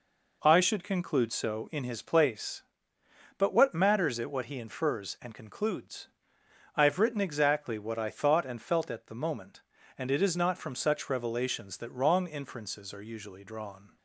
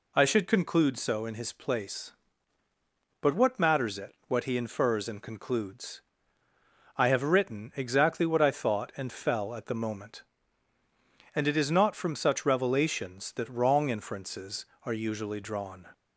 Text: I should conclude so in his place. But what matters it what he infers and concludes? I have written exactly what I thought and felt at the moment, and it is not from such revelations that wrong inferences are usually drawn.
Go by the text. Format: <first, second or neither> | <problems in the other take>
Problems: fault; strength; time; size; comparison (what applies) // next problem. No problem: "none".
first | says "fell" for "felt"; at 9.1 s